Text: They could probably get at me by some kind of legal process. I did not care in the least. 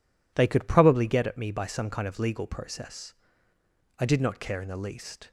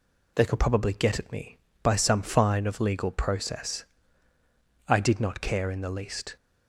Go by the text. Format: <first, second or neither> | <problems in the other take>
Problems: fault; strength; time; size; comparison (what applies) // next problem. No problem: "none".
first | says "fine" for "kind"; at 2.2 s